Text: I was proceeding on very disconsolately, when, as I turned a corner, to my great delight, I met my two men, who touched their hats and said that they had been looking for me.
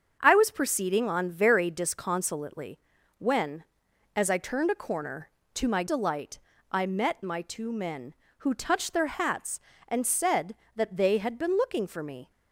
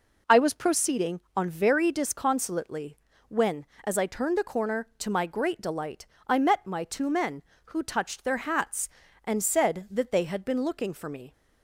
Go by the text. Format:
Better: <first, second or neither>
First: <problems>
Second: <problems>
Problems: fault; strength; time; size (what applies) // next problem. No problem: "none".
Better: second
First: starts louder than the rest; until 1.2 s; 7 dB // skips "great"; at 5.8 s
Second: none